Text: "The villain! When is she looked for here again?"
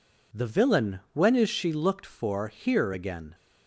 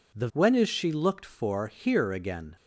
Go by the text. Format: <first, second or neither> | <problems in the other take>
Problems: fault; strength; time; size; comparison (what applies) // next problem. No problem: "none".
first | skips "villain"; at 0.3 s